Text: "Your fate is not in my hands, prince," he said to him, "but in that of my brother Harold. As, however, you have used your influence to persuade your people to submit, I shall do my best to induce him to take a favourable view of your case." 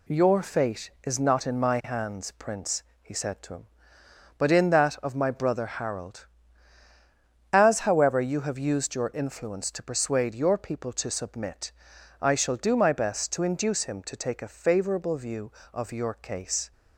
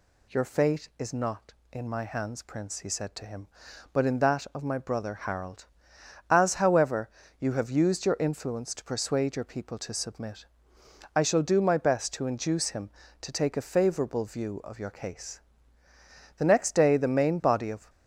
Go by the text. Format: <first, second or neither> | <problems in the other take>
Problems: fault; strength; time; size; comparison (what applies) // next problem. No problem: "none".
first | goes on to say "The next day the main body of"; from 16.3 s on; 1.5 s long